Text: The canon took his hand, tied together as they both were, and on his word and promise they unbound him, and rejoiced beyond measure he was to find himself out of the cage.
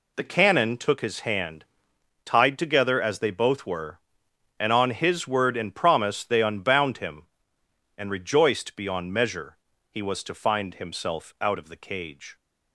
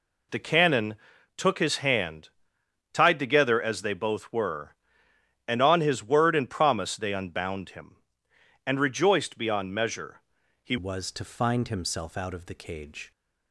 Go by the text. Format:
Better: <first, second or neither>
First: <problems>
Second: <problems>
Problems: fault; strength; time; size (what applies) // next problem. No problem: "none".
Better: first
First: pauses between "measure" and "he"; slight; at 9.5 s; 0.32 s long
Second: pauses between "canon" and "took"; at 0.9 s; 0.42 s long // pauses between "measure" and "he"; at 10.1 s; 0.42 s long // changes voice at "was"; from 10.7 s on; 2.4 s long